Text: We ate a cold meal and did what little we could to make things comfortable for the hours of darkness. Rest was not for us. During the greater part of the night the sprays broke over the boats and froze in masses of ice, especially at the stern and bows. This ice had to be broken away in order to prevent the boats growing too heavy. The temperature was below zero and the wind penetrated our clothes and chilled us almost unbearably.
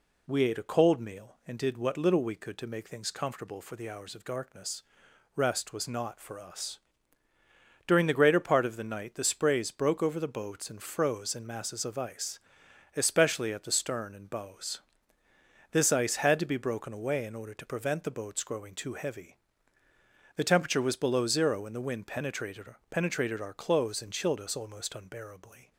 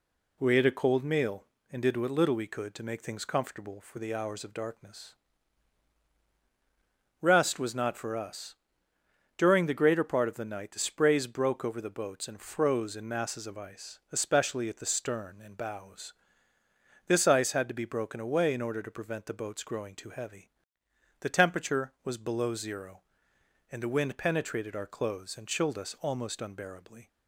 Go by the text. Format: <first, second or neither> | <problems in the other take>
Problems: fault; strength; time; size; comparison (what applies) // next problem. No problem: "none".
second | says "penetrated" twice; at 22.9 s